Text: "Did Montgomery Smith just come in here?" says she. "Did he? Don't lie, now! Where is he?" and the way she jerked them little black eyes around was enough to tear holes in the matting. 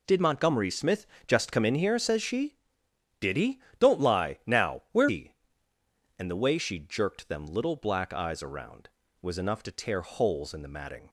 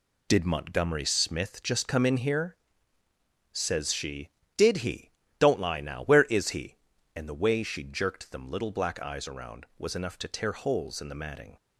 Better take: second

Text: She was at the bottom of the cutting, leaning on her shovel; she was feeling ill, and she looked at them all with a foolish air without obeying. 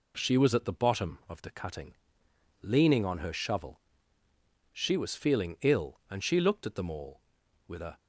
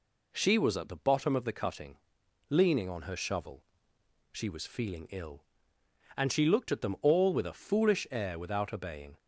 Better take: second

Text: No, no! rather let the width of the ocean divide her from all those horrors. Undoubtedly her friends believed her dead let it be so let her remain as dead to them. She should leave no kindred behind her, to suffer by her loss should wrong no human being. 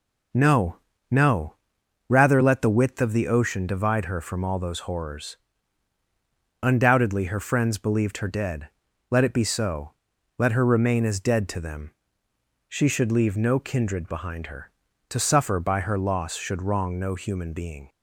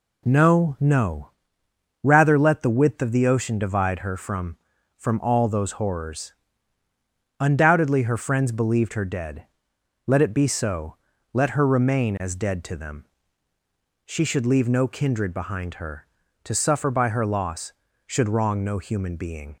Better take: first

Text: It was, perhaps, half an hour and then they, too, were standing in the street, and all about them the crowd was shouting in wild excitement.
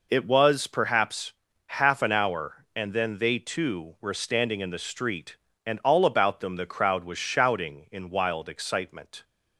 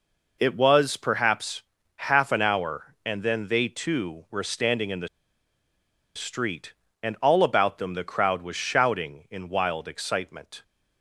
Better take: first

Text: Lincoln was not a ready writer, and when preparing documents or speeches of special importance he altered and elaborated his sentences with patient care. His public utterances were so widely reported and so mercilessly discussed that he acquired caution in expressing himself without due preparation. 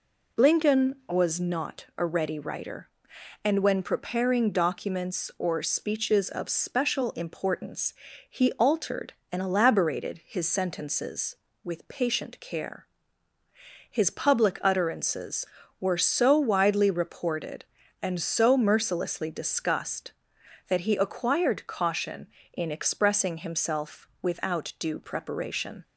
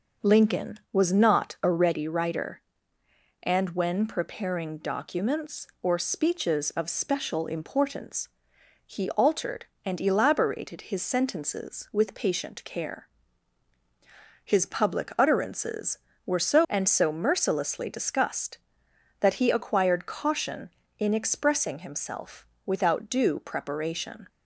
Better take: first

